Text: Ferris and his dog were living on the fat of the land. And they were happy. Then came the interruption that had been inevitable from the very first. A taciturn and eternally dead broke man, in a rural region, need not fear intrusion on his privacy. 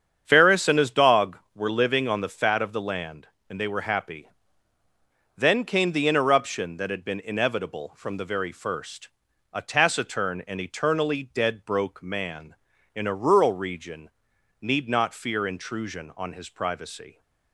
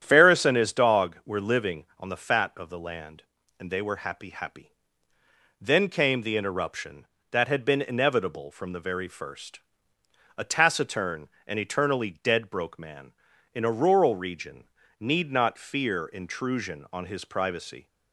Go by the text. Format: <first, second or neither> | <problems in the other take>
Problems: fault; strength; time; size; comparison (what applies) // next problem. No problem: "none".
first | starts louder than the rest; strong; until 1.0 s; 10 dB; strong in the first // says "happy" twice; at 4.3 s